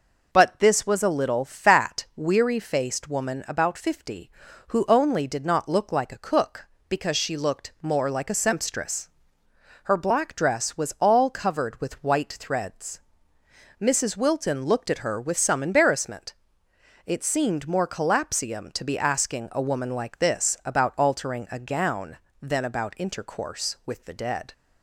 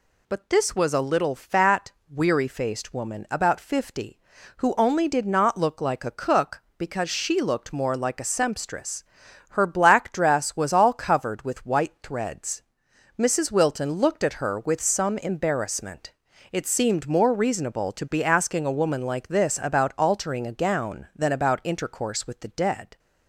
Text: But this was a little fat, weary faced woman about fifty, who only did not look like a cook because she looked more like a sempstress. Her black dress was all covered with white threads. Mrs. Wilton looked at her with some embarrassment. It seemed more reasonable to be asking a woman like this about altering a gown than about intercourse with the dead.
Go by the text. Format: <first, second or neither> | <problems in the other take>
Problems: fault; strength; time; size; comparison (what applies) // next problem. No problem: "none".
second | says "collapsium" for "reasonable"; at 17.8 s